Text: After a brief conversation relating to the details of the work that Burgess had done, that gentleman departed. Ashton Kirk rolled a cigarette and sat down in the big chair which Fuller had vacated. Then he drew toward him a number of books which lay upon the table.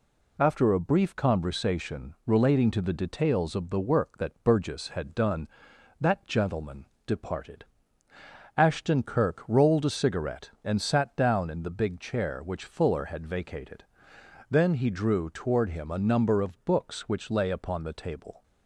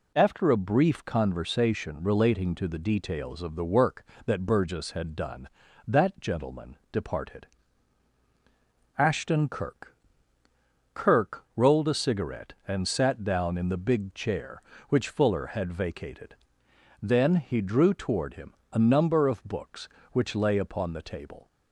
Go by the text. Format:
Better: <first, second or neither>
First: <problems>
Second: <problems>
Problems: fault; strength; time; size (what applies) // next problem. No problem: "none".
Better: first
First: pauses between "gentleman" and "departed"; slight; at 6.8 s; 0.22 s long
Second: pauses between "gentleman" and "departed"; slight; at 6.7 s; 0.16 s long // says "Kirk" twice; at 10.9 s // pauses between "him" and "a"; slight; at 18.5 s; 0.20 s long